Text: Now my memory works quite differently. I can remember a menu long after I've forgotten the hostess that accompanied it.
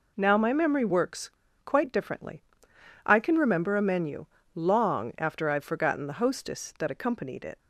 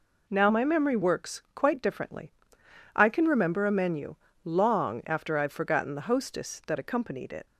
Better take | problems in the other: second | pauses between "works" and "quite"; slight; at 1.2 s; 0.33 s long // pauses between "menu" and "long"; slight; at 4.2 s; 0.30 s long; slight in the second

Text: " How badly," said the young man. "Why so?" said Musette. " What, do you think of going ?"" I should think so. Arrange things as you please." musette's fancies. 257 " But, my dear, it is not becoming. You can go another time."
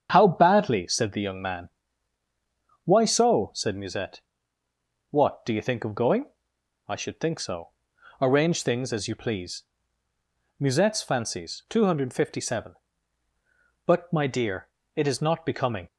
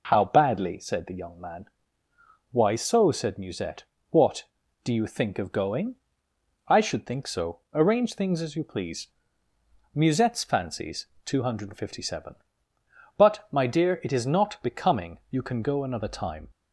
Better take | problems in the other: second | starts louder than the rest; strong; until 1.1 s; 8 dB // stops before "You can go another time"; at 15.8 s

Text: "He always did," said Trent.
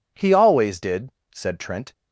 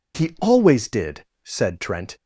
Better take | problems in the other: neither | none

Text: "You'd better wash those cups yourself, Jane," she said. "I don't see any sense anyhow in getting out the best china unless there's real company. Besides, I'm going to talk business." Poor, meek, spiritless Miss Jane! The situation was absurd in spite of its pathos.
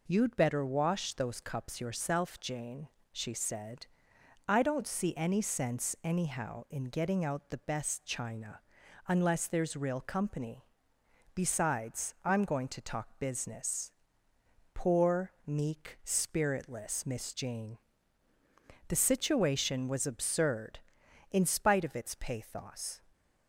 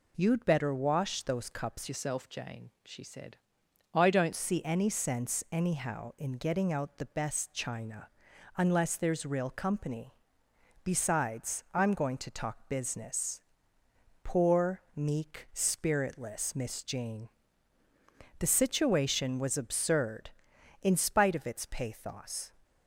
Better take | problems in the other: first | changes voice from "yourself" to "don't"; from 1.8 to 4.3 s; 2.5 s long // pauses between "china" and "unless"; noticeable; at 8.0 s; 0.48 s long; noticeable in the first

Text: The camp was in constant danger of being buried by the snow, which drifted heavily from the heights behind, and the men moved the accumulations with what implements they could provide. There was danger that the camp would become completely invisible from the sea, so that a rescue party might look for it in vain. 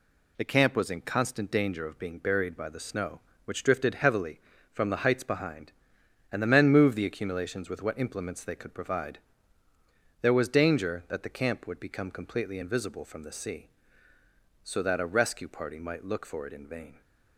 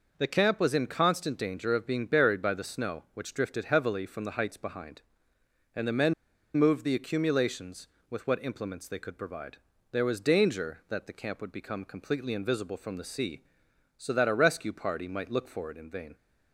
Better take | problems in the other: first | pauses between "men" and "moved"; at 6.1 s; 0.43 s long

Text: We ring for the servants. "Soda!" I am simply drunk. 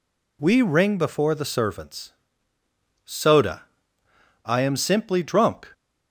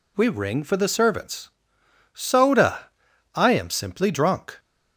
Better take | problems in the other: second | says "before" for "for"; at 0.9 s

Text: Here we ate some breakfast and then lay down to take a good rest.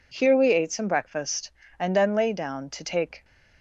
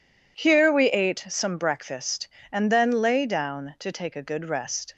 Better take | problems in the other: second | stops before "a good rest"; at 3.2 s

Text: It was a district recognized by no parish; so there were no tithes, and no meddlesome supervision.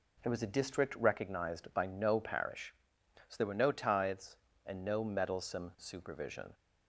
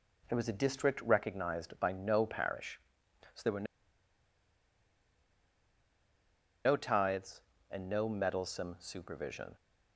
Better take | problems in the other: first | pauses between "were" and "no"; strong; at 3.6 s; 3.0 s long

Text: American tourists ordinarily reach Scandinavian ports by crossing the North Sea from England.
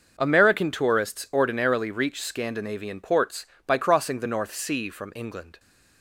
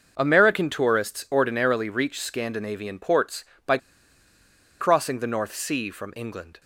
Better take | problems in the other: first | starts louder than the rest; noticeable; until 1.1 s; 6 dB; noticeable in the first // pauses between "by" and "crossing"; at 3.7 s; 1.0 s long

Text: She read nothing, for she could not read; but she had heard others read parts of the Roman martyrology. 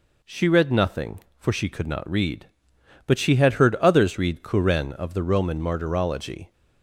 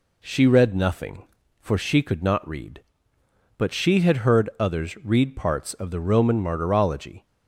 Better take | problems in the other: second | says "kuren" for "parts"; at 4.4 s

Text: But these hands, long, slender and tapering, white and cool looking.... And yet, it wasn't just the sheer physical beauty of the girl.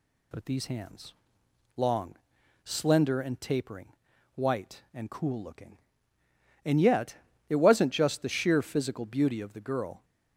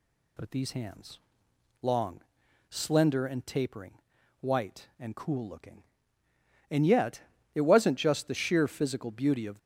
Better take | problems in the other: first | stops before "the girl"; at 9.5 s

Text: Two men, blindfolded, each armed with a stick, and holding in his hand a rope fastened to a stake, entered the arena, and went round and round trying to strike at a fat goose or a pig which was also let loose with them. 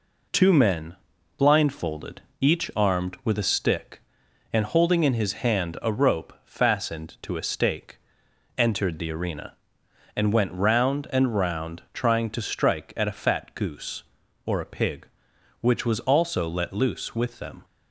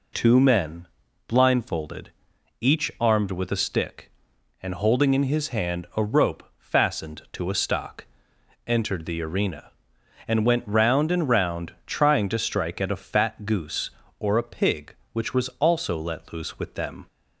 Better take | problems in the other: first | says "stock" for "stake"; at 7.5 s

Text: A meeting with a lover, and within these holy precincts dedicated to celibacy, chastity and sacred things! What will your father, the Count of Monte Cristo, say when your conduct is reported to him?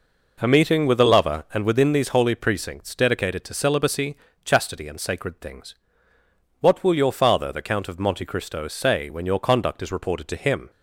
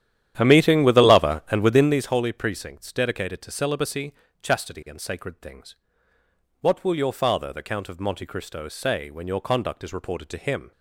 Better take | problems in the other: first | starts louder than the rest; strong; until 2.1 s; 11 dB

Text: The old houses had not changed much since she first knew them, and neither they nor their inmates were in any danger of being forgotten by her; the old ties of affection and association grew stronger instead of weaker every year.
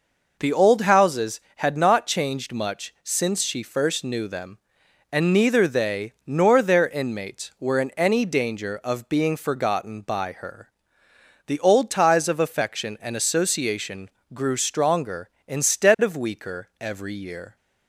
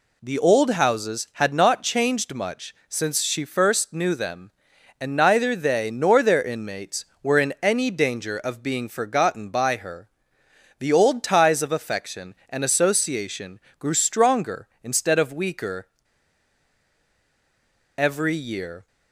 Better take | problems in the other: first | pauses between "much" and "since"; slight; at 2.7 s; 0.16 s long // pauses between "association" and "grew"; slight; at 13.5 s; 0.18 s long; slight in the first // pauses between "weaker" and "every"; strong; at 15.8 s; 2.1 s long

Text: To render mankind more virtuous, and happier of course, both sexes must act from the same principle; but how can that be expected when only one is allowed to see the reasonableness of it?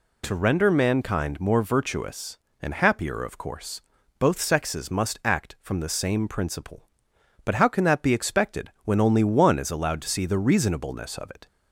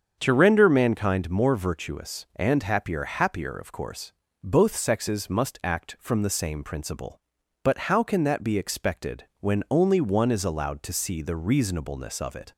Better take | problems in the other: first | starts louder than the rest; strong; until 1.2 s; 7 dB // says "happier" twice; at 3.0 s

